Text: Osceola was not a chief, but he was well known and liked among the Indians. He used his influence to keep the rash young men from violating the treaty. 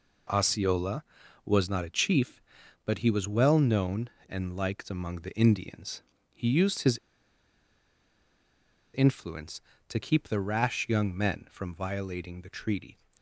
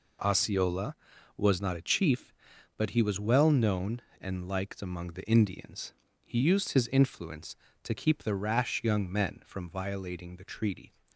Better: second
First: pauses between "his" and "influence"; strong; at 6.9 s; 1.9 s long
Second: none

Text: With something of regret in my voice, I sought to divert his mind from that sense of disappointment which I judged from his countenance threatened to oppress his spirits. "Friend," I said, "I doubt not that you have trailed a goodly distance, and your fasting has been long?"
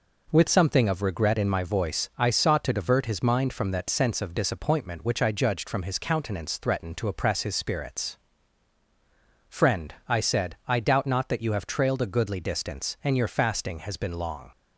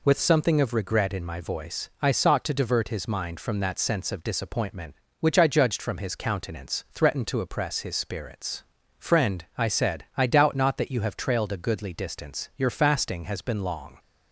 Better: first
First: none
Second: skips "and"; at 12.5 s

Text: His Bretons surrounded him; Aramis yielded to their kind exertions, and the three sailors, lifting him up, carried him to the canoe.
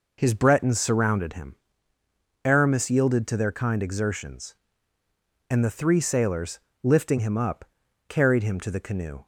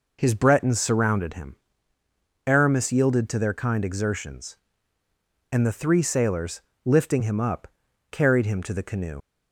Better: first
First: none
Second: leaves "canoe" unfinished; at 9.2 s; 80 ms

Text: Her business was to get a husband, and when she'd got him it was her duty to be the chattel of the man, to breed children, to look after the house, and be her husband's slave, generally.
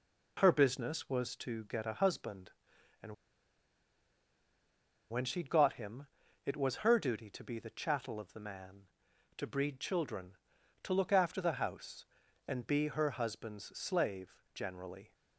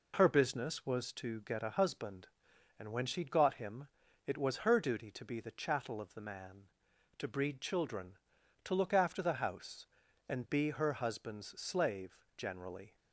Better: second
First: pauses between "and" and "when"; strong; at 3.1 s; 1.9 s long // pauses between "him" and "it"; at 6.0 s; 0.38 s long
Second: pauses between "him" and "it"; at 3.8 s; 0.38 s long

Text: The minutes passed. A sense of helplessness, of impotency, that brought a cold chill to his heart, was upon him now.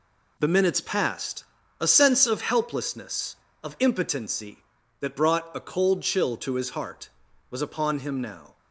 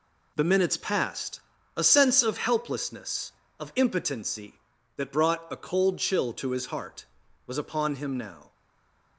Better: first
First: none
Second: stays silent after the last word; slight; from 8.5 s on; 0.6 s long

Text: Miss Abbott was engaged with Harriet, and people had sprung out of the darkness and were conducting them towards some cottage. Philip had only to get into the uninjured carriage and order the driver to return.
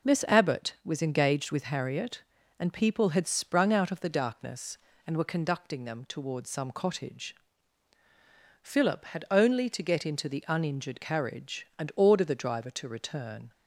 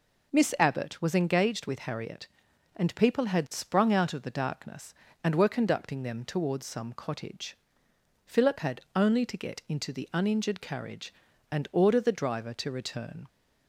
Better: neither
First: none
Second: none

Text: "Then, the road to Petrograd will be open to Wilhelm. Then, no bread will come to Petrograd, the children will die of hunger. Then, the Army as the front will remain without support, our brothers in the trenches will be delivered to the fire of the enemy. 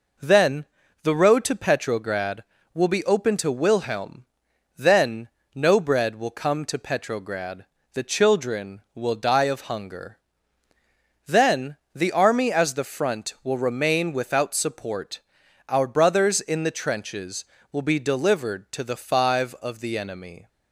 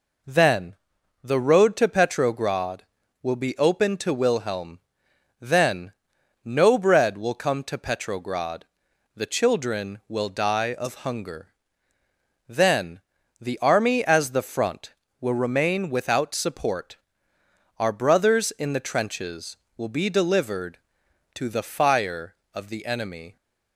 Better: second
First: says "five" for "fire"; at 18.9 s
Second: none

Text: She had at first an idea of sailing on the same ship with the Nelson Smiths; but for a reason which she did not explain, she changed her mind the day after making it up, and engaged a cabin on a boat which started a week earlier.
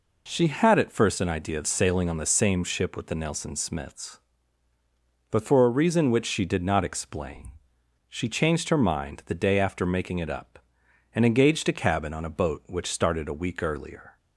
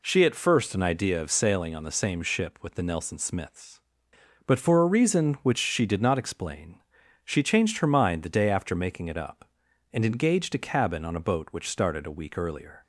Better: first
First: none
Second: skips "had"; at 0.2 s

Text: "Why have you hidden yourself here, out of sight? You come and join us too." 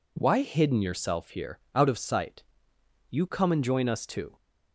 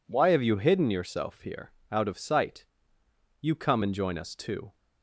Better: second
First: skips "have you"; at 0.4 s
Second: none

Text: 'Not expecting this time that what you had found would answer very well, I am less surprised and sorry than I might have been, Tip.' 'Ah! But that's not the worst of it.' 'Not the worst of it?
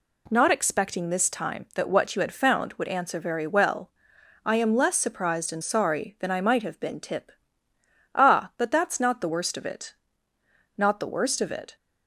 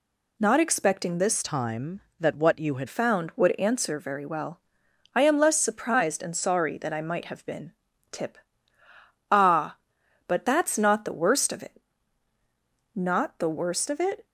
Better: first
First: none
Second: changes voice from "time" to "had"; from 1.4 to 2.8 s; 1.4 s long

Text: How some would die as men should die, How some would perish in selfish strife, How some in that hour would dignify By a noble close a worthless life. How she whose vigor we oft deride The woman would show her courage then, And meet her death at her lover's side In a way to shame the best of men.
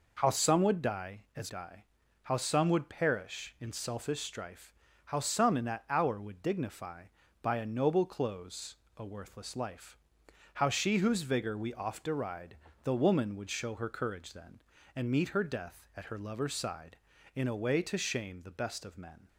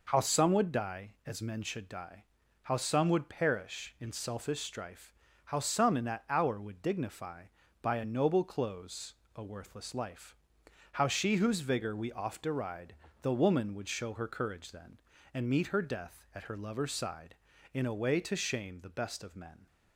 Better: second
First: skips "men should"; at 1.4 s // pauses between "close" and "a"; slight; at 8.7 s; 0.20 s long // pauses between "deride" and "The"; slight; at 12.5 s; 0.28 s long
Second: pauses between "close" and "a"; slight; at 9.1 s; 0.20 s long // pauses between "deride" and "The"; slight; at 12.9 s; 0.28 s long

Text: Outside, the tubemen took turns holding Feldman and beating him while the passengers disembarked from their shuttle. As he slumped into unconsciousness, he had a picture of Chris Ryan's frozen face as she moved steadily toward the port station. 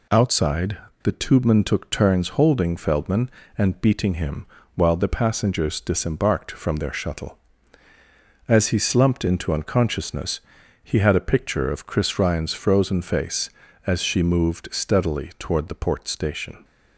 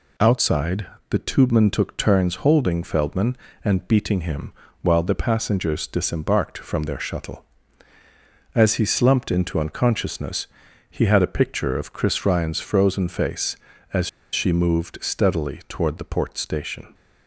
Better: first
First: pauses between "him" and "while"; slight; at 4.4 s; 0.30 s long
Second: pauses between "him" and "while"; slight; at 4.5 s; 0.30 s long // pauses between "as" and "she"; slight; at 14.0 s; 0.24 s long

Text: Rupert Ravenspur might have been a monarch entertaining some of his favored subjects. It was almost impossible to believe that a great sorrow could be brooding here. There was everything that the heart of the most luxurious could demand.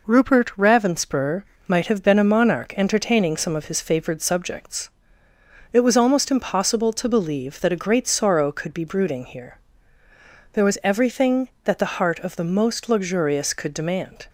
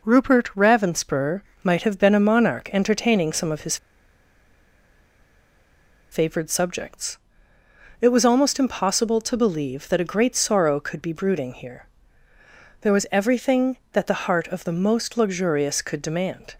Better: first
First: pauses between "Ravenspur" and "might"; slight; at 1.4 s; 0.22 s long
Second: pauses between "Ravenspur" and "might"; slight; at 1.4 s; 0.20 s long // pauses between "his" and "favored"; strong; at 3.7 s; 2.3 s long

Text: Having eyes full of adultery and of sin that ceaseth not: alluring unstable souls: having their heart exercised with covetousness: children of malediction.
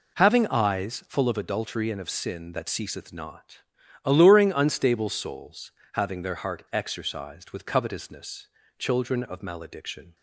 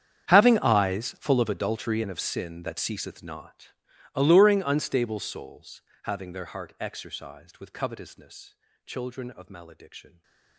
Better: first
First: none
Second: gets quieter; strong; throughout; 21 dB // stays silent after the last word; slight; from 10.0 s on; 0.5 s long

